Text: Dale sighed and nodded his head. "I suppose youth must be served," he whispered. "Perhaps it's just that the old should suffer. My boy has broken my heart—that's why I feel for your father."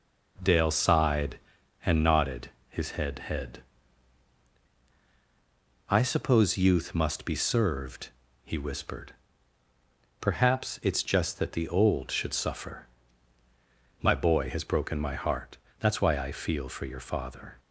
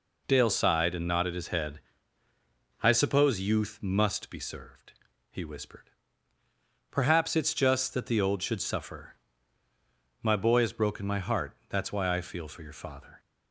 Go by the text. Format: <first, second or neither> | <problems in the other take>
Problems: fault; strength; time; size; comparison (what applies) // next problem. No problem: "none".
second | pauses between "nodded" and "his"; slight; at 2.5 s; 0.18 s long // says "head" twice; at 3.2 s